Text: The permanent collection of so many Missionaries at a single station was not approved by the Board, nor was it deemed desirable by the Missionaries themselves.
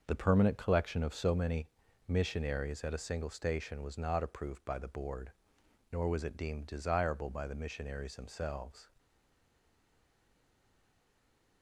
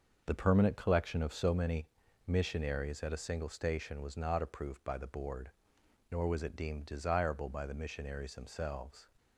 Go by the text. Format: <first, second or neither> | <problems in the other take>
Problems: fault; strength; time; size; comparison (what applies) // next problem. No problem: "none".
second | starts louder than the rest; until 1.0 s; 6 dB; also in the second // pauses between "many" and "Missionaries"; at 1.6 s; 0.40 s long; also in the second // stays silent after the last word; strong; from 8.9 s on; 2.7 s long